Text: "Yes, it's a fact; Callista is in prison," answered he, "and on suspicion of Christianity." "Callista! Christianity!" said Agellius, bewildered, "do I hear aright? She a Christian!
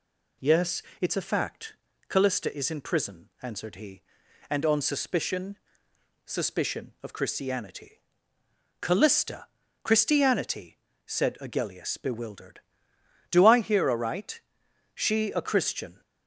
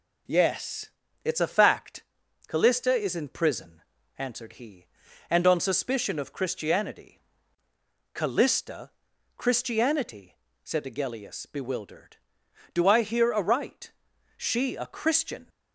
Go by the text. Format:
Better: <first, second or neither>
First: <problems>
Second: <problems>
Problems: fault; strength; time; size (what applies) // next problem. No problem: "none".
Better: second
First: says "suspicion" twice; at 6.2 s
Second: none